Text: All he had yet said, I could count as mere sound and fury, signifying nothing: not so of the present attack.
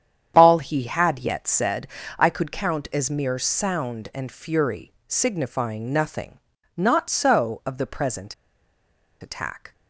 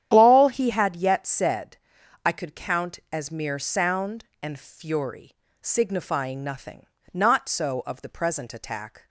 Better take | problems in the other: second | starts louder than the rest; strong; until 1.3 s; 9 dB; strong in the second // pauses between "present" and "attack"; noticeable; at 8.3 s; 0.87 s long

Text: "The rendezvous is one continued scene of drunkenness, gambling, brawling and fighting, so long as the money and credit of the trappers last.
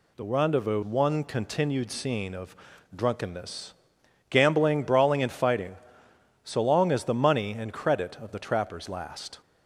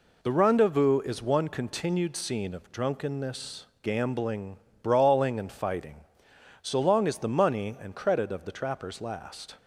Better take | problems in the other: second | skips "is"; at 0.8 s // pauses between "of" and "drunkenness"; at 2.5 s; 0.40 s long

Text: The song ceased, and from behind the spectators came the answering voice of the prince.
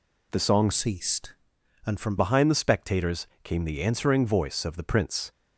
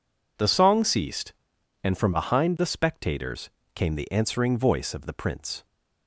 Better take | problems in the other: second | changes voice from "ceased" to "from"; from 0.7 to 2.1 s; 1.4 s long // pauses between "spectators" and "came"; slight; at 3.2 s; 0.16 s long; slight in the second

